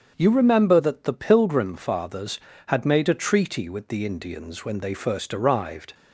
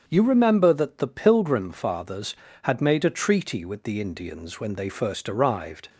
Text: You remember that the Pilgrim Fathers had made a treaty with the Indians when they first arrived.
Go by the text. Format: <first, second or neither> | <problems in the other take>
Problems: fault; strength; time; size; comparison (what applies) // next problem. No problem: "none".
neither | starts louder than the rest; strong; the same in both